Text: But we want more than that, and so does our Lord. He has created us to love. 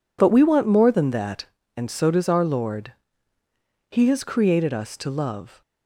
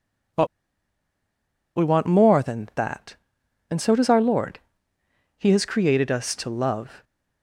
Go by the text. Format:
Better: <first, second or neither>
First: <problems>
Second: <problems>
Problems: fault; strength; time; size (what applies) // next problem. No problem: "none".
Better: first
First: none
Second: pauses between "But" and "we"; strong; at 0.4 s; 1.3 s long